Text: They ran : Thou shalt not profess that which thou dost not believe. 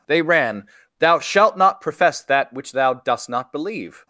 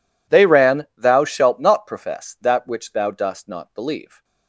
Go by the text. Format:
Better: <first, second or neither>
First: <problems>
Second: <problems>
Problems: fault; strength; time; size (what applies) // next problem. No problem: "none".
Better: neither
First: none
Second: none